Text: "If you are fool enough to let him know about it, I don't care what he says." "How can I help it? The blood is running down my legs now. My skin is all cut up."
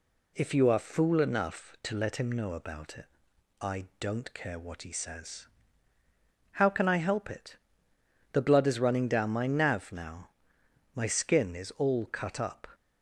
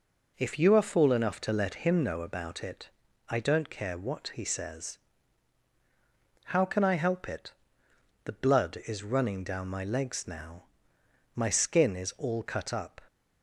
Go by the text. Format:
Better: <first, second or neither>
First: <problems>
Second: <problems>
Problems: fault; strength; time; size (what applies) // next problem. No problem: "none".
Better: second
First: says "nav" for "legs"; at 9.4 s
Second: none